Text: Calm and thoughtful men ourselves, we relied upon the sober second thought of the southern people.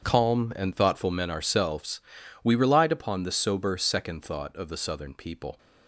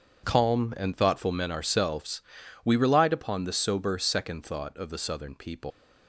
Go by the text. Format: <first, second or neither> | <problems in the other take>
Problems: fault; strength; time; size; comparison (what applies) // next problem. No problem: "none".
first | starts louder than the rest; until 1.2 s; 7 dB; strong in the first // leaves "people" unfinished; at 5.7 s; 80 ms